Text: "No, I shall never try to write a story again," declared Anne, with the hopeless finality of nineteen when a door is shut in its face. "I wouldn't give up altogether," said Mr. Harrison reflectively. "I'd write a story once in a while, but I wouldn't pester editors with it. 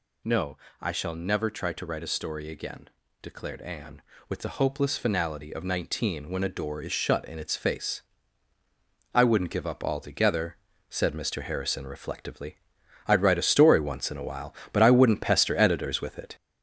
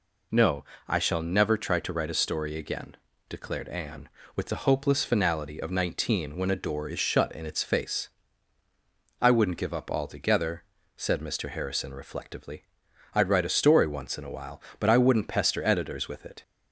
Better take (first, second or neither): second